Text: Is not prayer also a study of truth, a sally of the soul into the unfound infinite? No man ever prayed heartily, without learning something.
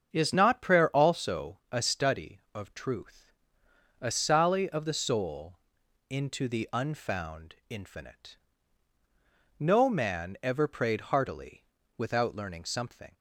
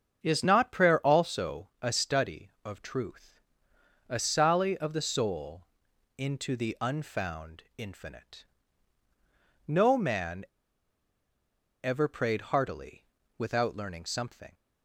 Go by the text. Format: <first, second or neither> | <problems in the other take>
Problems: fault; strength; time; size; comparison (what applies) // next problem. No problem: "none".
first | starts louder than the rest; strong; until 1.2 s; 7 dB; strong in the first // pauses between "soul" and "into"; noticeable; at 5.6 s; 0.52 s long; noticeable in the first // pauses between "man" and "ever"; strong; at 10.4 s; 1.3 s long